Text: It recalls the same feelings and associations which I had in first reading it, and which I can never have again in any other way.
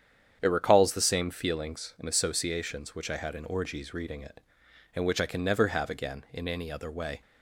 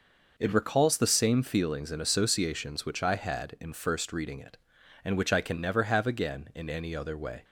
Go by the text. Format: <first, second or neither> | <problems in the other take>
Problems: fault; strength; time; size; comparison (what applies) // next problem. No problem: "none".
second | starts louder than the rest; strong; until 1.4 s; 8.5 dB // says "orgies" for "first"; at 3.4 s